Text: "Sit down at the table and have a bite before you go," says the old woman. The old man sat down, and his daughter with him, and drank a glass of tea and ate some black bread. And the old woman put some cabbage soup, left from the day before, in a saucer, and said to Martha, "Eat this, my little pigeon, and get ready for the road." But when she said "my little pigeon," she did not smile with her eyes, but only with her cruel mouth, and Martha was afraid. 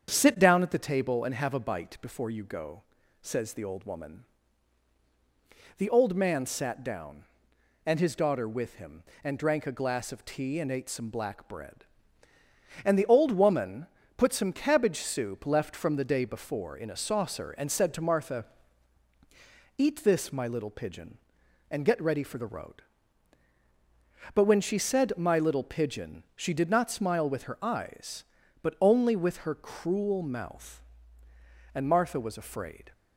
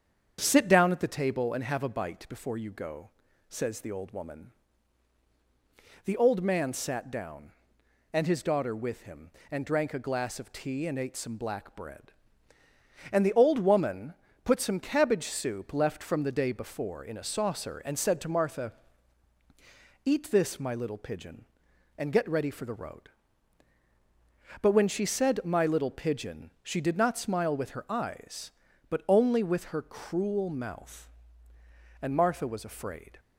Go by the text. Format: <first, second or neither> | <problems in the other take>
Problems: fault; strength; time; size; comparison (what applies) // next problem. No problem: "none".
neither | starts louder than the rest; strong; the same in both // pauses between "woman" and "put"; slight; the same in both